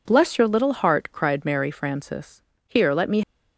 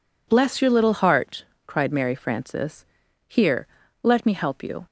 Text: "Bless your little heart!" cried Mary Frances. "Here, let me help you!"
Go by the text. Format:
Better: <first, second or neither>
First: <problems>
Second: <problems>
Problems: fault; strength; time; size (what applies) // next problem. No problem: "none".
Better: second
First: stops before "help you"; at 3.2 s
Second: none